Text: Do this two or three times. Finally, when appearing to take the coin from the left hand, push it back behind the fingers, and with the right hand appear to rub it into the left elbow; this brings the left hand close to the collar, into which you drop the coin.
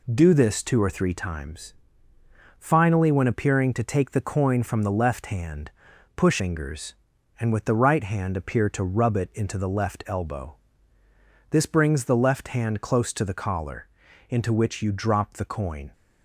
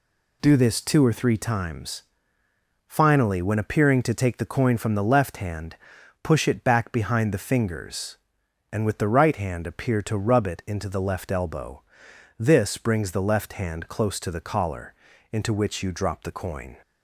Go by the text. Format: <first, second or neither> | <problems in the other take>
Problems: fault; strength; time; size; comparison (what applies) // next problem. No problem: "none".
second | skips "it back behind the"; at 6.3 s